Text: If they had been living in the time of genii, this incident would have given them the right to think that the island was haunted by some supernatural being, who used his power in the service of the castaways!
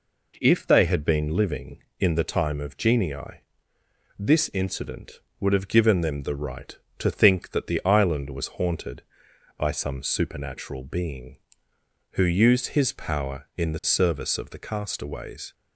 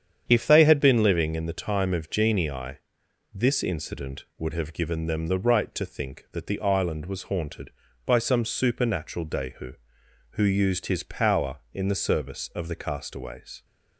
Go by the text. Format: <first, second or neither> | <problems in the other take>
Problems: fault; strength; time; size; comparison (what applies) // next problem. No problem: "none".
first | starts louder than the rest; strong; until 1.2 s; 8.5 dB // says "dehu" for "being"; at 9.2 s